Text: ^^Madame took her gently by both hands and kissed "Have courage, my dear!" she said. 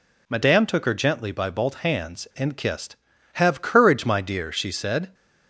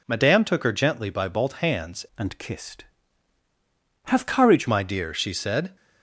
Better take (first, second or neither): first